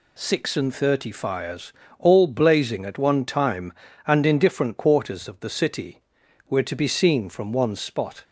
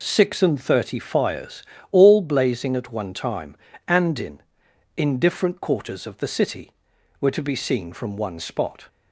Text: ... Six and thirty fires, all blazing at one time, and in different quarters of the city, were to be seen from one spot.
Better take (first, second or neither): first